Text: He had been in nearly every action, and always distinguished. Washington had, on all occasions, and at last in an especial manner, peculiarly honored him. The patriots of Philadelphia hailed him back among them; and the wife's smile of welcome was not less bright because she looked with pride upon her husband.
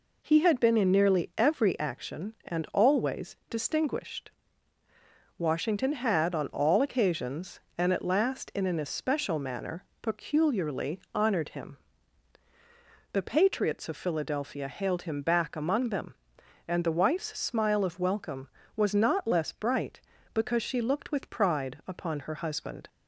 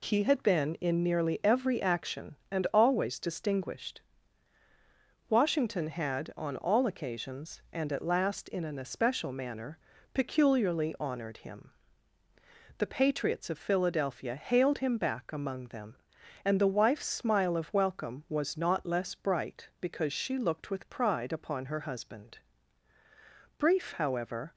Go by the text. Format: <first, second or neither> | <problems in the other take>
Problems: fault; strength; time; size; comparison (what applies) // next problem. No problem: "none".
first | goes on to say "Brief however"; noticeable; from 23.5 s on; 0.96 s long